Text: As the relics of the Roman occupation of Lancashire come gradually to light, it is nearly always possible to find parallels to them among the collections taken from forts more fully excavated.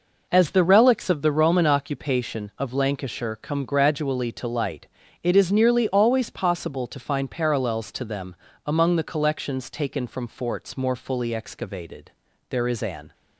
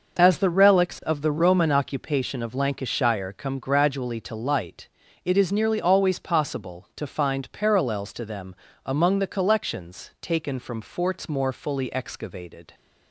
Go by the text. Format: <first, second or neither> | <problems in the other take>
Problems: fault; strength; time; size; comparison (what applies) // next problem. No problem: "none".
second | pauses between "them" and "among"; slight; at 8.3 s; 0.32 s long; slight in the second // goes on to say "There is an"; noticeable; from 12.4 s on; 0.64 s long